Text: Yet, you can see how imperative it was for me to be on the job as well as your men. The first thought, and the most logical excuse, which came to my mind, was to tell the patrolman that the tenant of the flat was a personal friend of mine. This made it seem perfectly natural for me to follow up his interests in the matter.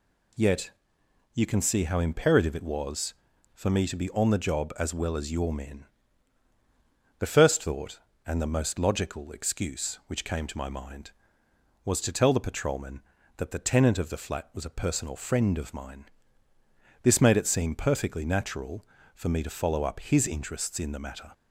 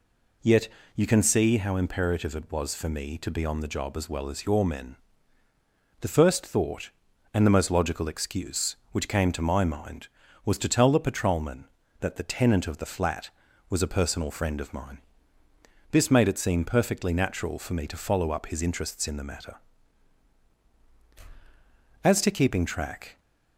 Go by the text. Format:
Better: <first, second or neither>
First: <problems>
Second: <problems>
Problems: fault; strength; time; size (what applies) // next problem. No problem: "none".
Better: first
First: none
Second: goes on to say "As to keeping track"; noticeable; from 22.0 s on; 1.1 s long